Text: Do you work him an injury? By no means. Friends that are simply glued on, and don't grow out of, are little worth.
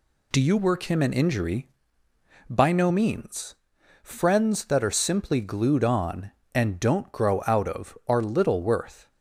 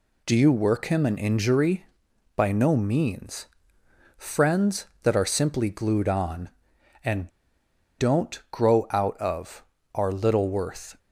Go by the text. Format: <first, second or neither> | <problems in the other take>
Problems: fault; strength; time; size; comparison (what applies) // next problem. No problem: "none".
first | pauses between "and" and "don't"; noticeable; at 7.2 s; 0.70 s long